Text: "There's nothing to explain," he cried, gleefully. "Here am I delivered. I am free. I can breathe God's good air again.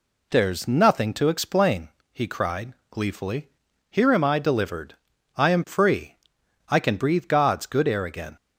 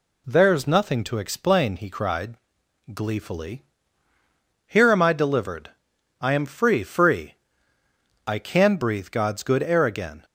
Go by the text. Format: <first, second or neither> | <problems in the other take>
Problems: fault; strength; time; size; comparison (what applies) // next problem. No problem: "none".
first | says "free" twice; at 6.8 s